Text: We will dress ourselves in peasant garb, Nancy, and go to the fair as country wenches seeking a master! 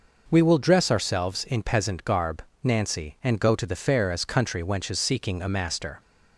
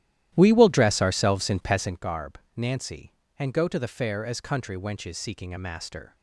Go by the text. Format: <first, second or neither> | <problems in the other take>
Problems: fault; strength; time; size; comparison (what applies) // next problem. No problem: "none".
first | starts louder than the rest; strong; until 2.0 s; 13 dB